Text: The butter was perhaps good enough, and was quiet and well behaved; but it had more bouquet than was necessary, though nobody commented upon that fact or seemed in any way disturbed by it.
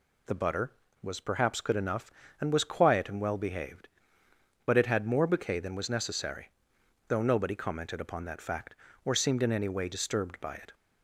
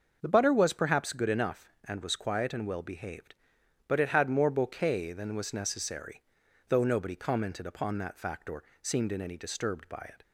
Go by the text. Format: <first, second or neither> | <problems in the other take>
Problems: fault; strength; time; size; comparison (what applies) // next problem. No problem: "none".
first | starts louder than the rest; until 1.2 s; 6 dB // pauses between "or" and "seemed"; slight; at 8.6 s; 0.20 s long // skips "way"; at 9.3 s